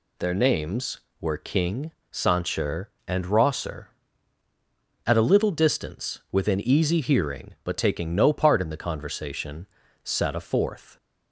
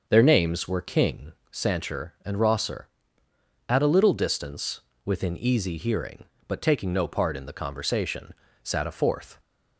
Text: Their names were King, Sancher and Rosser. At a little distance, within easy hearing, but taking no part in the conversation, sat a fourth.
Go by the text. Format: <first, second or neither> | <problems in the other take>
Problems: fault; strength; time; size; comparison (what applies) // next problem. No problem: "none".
first | starts louder than the rest; until 1.2 s; 6.5 dB